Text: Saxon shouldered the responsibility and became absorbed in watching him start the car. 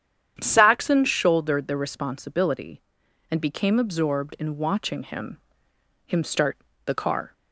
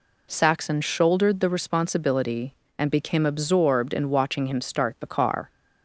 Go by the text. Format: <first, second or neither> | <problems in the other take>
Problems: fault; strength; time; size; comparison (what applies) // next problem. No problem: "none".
second | starts louder than the rest; strong; until 1.4 s; 9 dB // says "him" twice; at 6.0 s // pauses between "start" and "the"; slight; at 6.5 s; 0.28 s long